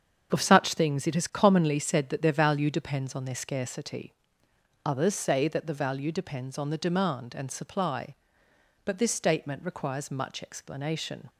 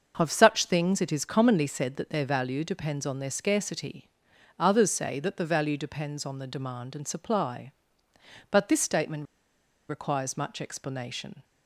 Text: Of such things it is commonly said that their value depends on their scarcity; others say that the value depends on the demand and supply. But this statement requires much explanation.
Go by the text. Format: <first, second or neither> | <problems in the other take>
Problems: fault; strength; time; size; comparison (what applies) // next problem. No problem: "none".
first | starts louder than the rest; until 1.1 s; 6.5 dB; strong in the first // pauses between "statement" and "requires"; noticeable; at 9.2 s; 0.63 s long